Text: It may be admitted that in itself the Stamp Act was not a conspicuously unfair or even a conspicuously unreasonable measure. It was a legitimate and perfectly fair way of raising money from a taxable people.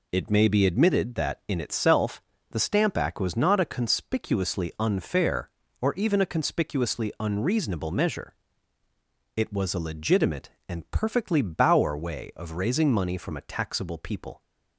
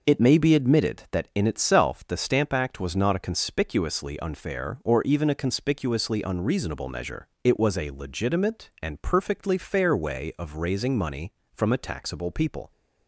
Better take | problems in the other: second | pauses between "itself" and "the"; slight; at 2.2 s; 0.30 s long // says "bauer" for "fair"; at 11.4 s

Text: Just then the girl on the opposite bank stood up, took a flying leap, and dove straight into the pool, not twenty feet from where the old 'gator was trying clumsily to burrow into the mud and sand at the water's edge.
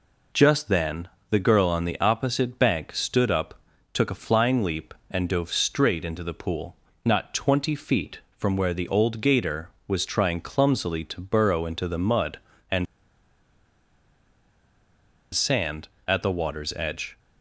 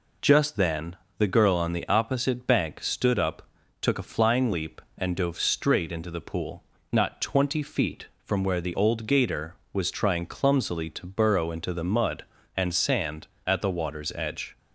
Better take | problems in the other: second | pauses between "then" and "the"; slight; at 1.0 s; 0.20 s long; slight in the second // pauses between "and" and "sand"; strong; at 12.8 s; 2.4 s long

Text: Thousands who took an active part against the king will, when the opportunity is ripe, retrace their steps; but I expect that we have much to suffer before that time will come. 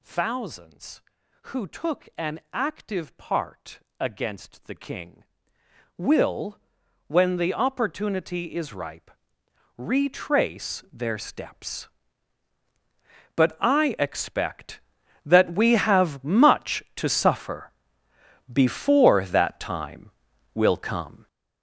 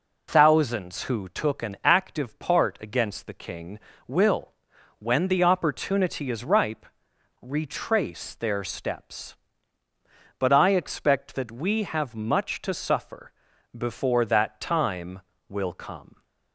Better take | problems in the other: second | gets louder; strong; throughout; 10.5 dB // pauses between "part" and "against"; slight; at 3.7 s; 0.20 s long // pauses between "suffer" and "before"; noticeable; at 17.7 s; 0.80 s long; noticeable in the second

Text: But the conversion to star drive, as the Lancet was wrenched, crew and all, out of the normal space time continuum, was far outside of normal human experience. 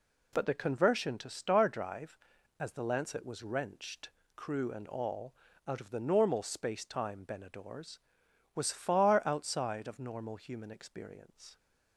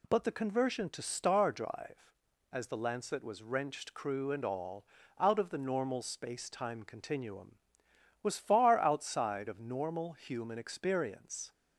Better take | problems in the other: second | says "benadors" for "continuum"; at 7.2 s

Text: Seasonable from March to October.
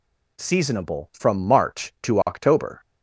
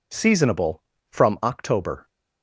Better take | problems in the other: first | skips "March to"; at 1.4 s

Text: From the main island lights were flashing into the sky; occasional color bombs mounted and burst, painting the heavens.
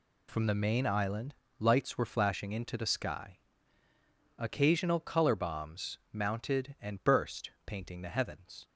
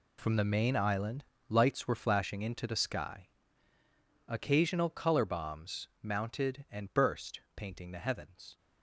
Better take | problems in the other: first | gets quieter; strong; throughout; 13 dB // pauses between "island" and "lights"; slight; at 1.2 s; 0.24 s long; slight in the first

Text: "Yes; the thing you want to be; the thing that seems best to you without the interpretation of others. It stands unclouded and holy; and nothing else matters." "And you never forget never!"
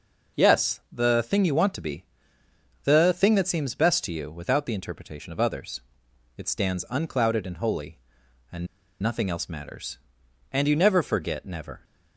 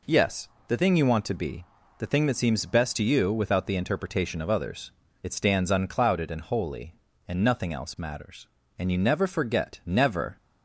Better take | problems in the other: second | pauses between "and" and "nothing"; slight; at 8.6 s; 0.34 s long

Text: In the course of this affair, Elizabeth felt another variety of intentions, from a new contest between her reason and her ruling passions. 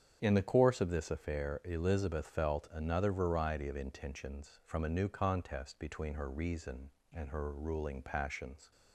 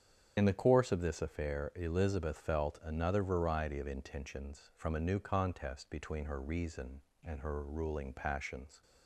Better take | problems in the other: first | loses the start of "In"; at 0.3 s; 55 ms // starts louder than the rest; strong; until 1.3 s; 8 dB; strong in the first

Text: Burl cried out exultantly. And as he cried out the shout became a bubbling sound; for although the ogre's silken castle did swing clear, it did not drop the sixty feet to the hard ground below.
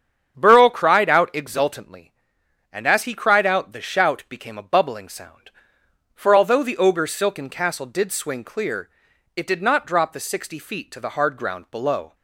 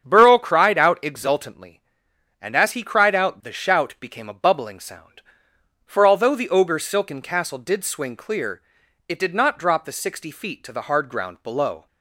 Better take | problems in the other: neither | starts louder than the rest; strong; the same in both

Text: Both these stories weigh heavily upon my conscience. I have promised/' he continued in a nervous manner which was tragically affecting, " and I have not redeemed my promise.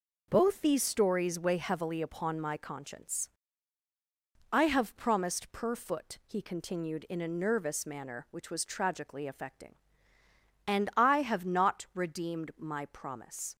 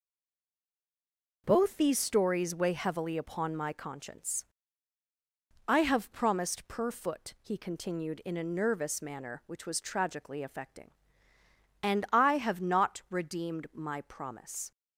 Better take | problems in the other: first | stays silent before the first word; noticeable; until 1.4 s; 1.4 s long

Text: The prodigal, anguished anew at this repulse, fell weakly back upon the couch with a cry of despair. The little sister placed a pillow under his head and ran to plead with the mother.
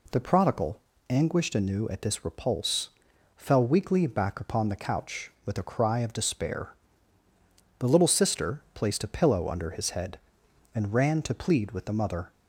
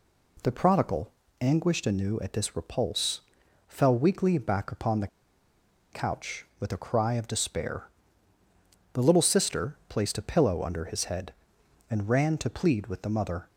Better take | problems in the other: first | pauses between "the" and "couch"; noticeable; at 5.0 s; 0.84 s long

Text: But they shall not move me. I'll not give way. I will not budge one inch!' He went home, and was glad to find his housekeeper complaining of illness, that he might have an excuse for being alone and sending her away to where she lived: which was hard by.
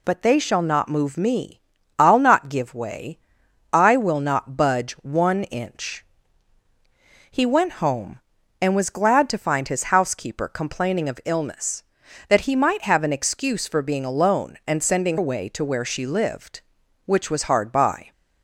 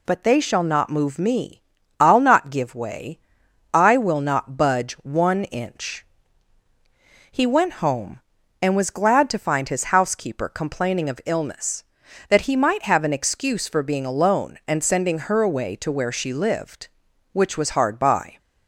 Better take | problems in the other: second | skips "her"; at 15.1 s

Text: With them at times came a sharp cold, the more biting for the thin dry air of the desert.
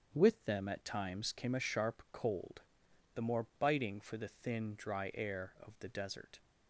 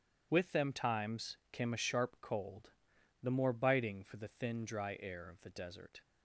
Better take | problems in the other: first | starts louder than the rest; strong; until 1.3 s; 9.5 dB; strong in the first // skips "at"; at 0.7 s

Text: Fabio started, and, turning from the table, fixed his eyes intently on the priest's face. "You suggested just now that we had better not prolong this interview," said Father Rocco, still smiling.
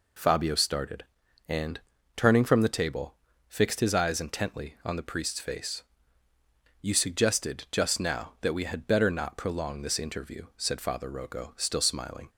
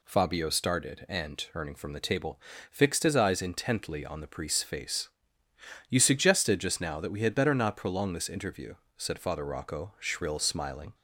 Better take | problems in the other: first | says "shrill" for "still"; at 9.9 s

